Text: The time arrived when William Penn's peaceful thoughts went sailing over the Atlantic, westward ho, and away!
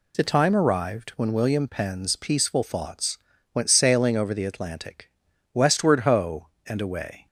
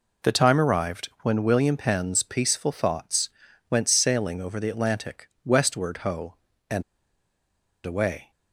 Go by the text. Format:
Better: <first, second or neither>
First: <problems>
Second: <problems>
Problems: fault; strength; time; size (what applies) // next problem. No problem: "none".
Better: first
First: pauses between "thoughts" and "went"; slight; at 3.1 s; 0.34 s long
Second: pauses between "thoughts" and "went"; at 3.2 s; 0.42 s long // pauses between "and" and "away"; at 6.8 s; 1.0 s long